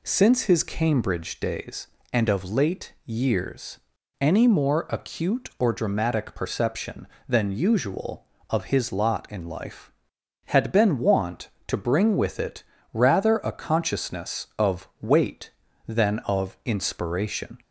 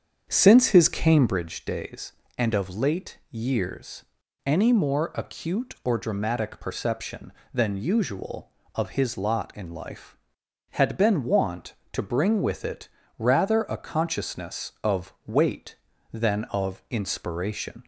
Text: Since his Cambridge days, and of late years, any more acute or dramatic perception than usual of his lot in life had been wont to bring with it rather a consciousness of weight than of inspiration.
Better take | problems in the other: first | starts louder than the rest; strong; until 1.4 s; 7.5 dB // pauses between "it" and "rather"; slight; at 12.8 s; 0.28 s long; slight in the first

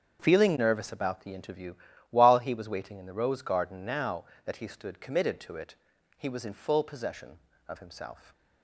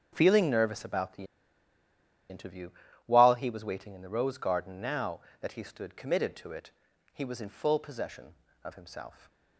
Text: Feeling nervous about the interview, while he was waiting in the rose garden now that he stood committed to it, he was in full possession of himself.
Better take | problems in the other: first | starts louder than the rest; strong; until 1.1 s; 7.5 dB; strong in the first // pauses between "the" and "interview"; at 1.2 s; 1.0 s long

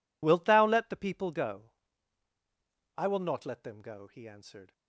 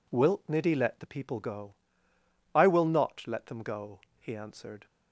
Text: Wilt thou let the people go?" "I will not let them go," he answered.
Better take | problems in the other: first | says "niddy" for "thou"; at 0.4 s

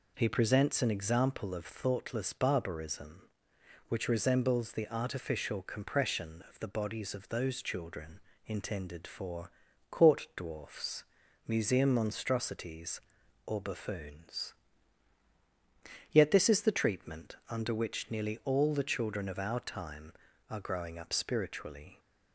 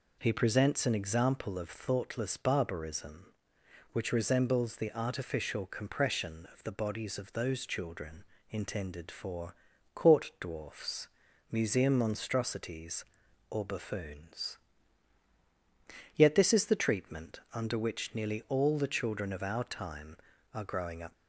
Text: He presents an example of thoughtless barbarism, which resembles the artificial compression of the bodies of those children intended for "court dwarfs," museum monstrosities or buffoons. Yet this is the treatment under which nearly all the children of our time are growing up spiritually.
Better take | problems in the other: first | pauses between "children" and "intended"; slight; at 8.2 s; 0.26 s long; slight in the first // pauses between "for" and "court"; at 9.5 s; 0.40 s long; also in the first // stops before "spiritually"; at 21.1 s

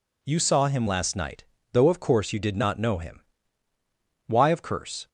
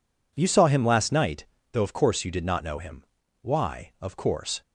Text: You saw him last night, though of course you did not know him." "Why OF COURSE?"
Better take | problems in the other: neither | none

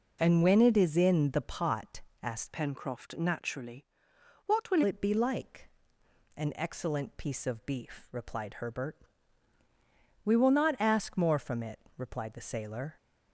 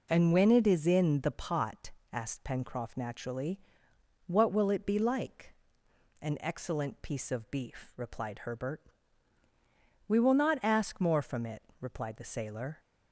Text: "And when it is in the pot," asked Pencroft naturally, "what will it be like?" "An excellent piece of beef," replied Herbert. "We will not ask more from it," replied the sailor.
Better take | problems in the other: second | changes voice from "Pencroft" to "will"; from 2.5 to 4.8 s; 2.3 s long

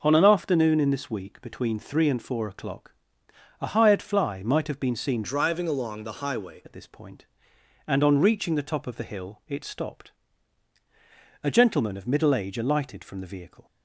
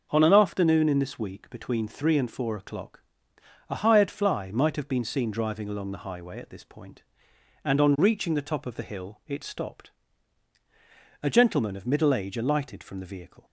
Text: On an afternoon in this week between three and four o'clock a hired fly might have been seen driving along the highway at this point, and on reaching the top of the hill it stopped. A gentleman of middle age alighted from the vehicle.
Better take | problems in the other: second | pauses between "o'clock" and "a"; noticeable; at 2.9 s; 0.68 s long; noticeable in the second // changes voice from "driving" to "highway"; from 5.2 to 6.6 s; 1.4 s long

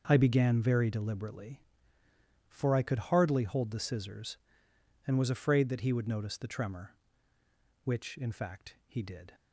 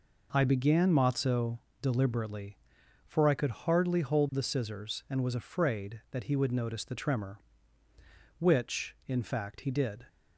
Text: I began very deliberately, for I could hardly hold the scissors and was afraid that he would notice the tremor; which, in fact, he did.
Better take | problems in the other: first | says "matzo" for "very"; at 0.9 s

